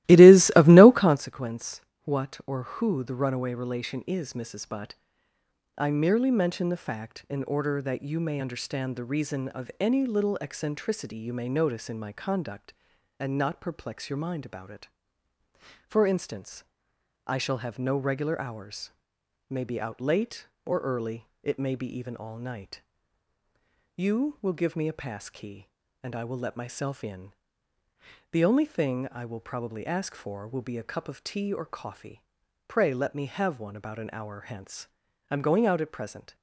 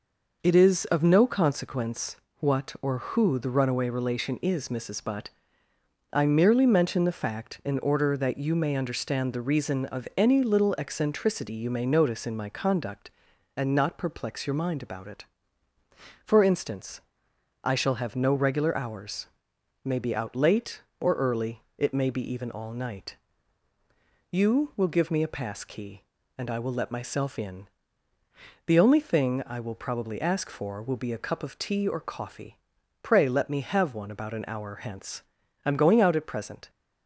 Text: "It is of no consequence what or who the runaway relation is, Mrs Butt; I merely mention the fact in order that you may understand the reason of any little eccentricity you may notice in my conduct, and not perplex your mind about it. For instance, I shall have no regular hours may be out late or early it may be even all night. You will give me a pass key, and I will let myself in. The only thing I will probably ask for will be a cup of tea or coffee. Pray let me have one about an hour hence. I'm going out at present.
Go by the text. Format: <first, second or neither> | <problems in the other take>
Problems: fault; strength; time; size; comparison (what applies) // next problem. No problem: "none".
second | starts louder than the rest; strong; until 1.3 s; 16.5 dB // pauses between "consequence" and "what"; slight; at 1.8 s; 0.22 s long; slight in the second // pauses between "hours" and "may"; noticeable; at 18.9 s; 0.58 s long; noticeable in the second // pauses between "early" and "it"; slight; at 21.2 s; 0.16 s long; slight in the second